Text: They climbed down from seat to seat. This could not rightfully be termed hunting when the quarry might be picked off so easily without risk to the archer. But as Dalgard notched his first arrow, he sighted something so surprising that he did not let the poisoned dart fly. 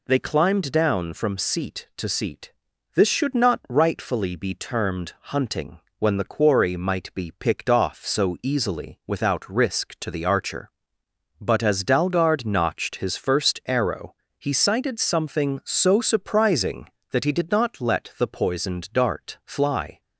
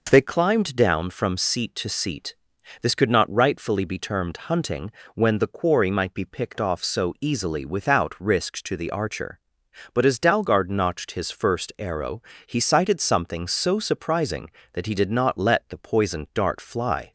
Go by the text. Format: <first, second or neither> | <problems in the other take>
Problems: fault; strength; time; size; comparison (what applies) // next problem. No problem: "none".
second | says "should" for "could"; at 3.0 s // pauses between "hunting" and "when"; slight; at 5.7 s; 0.20 s long; slight in the second